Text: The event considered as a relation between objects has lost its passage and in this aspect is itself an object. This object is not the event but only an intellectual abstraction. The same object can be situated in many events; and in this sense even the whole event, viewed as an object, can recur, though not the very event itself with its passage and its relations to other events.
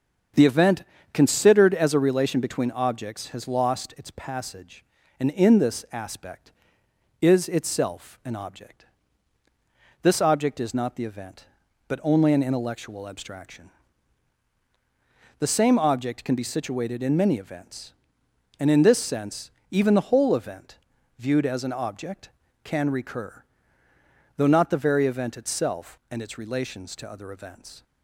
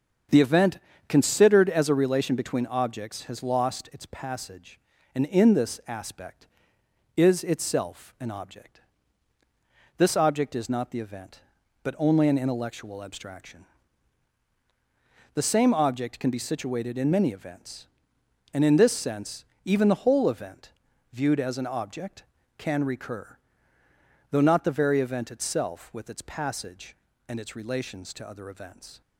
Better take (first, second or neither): second